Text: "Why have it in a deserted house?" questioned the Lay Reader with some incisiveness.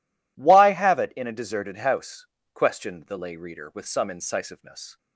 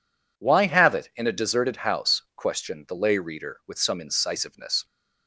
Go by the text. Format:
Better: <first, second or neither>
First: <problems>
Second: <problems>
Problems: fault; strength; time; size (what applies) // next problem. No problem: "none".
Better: neither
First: none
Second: none